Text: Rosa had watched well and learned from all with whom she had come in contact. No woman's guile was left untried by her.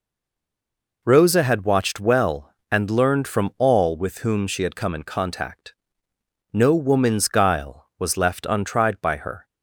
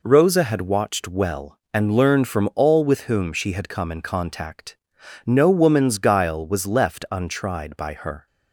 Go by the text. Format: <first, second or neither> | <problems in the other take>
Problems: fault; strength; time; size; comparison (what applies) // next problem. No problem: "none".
second | stays silent before the first word; until 1.0 s; 1.0 s long